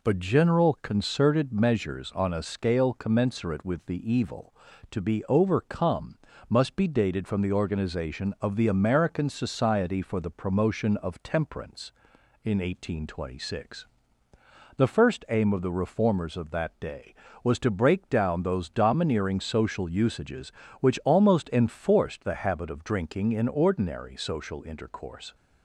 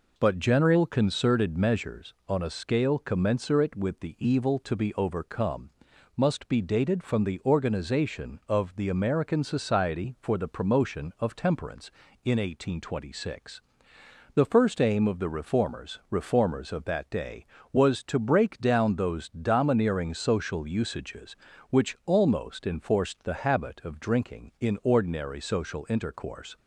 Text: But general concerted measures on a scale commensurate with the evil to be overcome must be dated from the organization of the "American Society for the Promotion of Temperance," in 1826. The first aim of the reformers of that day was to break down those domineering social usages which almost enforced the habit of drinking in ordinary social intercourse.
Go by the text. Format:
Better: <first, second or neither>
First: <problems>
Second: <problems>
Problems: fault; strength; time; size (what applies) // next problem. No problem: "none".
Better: first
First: pauses between "overcome" and "must"; slight; at 6.1 s; 0.32 s long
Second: pauses between "overcome" and "must"; noticeable; at 5.6 s; 0.46 s long // says "reformers" twice; at 16.0 s